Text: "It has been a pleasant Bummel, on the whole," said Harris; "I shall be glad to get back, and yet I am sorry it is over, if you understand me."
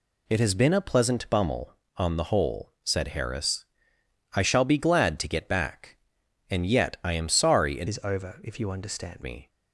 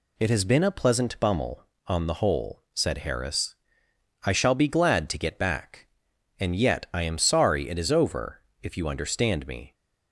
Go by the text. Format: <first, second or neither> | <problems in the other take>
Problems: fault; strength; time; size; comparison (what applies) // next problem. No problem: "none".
second | changes voice from "is" to "understand"; from 7.8 to 9.2 s; 1.4 s long